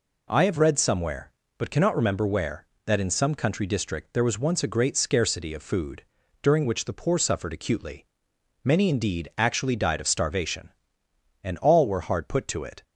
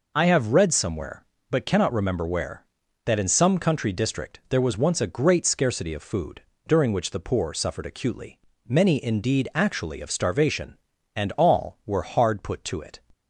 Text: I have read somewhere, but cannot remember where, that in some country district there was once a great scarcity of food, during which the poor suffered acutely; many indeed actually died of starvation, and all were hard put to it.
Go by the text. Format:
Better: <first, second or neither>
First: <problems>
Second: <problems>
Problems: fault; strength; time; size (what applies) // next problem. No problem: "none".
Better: first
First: none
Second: skips "died"; at 10.0 s